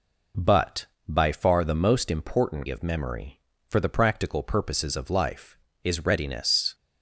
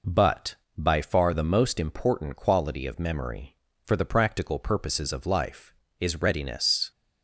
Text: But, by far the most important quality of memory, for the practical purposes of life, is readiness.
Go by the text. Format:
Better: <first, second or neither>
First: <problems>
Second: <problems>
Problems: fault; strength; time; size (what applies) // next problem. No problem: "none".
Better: second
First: skips "quality"; at 2.6 s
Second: none